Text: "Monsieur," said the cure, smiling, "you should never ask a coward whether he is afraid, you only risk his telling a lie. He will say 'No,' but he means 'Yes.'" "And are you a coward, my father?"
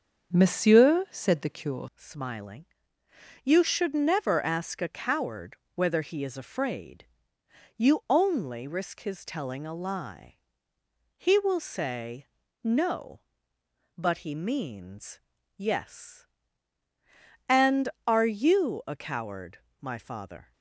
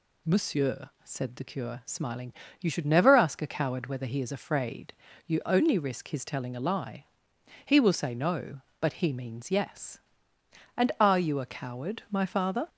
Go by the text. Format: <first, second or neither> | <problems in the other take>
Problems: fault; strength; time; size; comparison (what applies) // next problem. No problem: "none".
second | starts louder than the rest; strong; until 1.4 s; 7 dB // changes voice at "smiling"; from 1.9 s on; 18.6 s long // pauses between "coward" and "whether"; slight; at 5.5 s; 0.18 s long // pauses between "say" and "No"; slight; at 12.2 s; 0.36 s long // pauses between "means" and "Yes"; at 15.1 s; 0.38 s long